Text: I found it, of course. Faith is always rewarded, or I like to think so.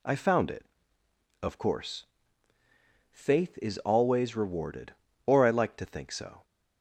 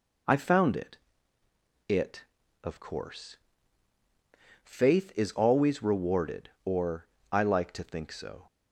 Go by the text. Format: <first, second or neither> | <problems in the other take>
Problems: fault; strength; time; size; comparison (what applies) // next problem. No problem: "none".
first | says "it" twice; at 1.8 s // pauses between "or" and "I"; slight; at 7.0 s; 0.26 s long